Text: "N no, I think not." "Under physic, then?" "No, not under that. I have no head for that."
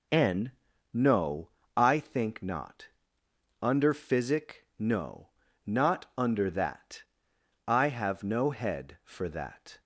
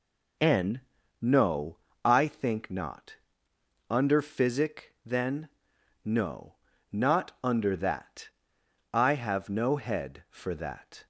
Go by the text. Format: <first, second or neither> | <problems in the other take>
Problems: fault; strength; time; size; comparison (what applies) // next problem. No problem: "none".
second | pauses between "N" and "no"; at 0.5 s; 0.38 s long; also in the second // skips "then"; at 4.7 s